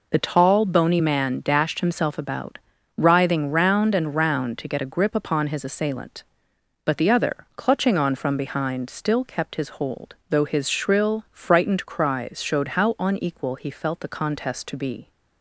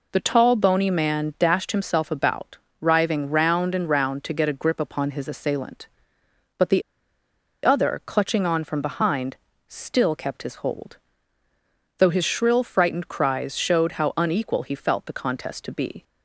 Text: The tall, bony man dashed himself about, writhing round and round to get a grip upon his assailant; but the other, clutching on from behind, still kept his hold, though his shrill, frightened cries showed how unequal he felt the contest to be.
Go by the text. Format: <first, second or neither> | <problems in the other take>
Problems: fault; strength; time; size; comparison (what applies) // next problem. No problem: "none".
first | pauses between "the" and "other"; noticeable; at 6.8 s; 0.81 s long